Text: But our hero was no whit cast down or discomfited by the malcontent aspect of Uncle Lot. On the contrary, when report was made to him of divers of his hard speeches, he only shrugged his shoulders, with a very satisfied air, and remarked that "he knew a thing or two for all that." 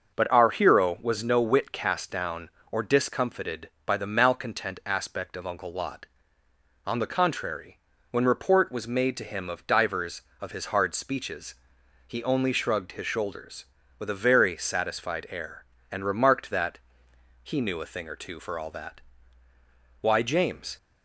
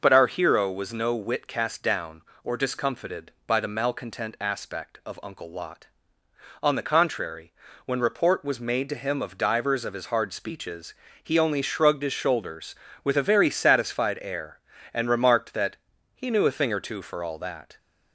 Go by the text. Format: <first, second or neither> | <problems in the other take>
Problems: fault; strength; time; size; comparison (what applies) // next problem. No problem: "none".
second | starts louder than the rest; noticeable; until 1.1 s; 6 dB // pauses between "that" and "he"; noticeable; at 16.7 s; 0.66 s long; also in the second // goes on to say "Why James"; noticeable; from 20.0 s on; 0.76 s long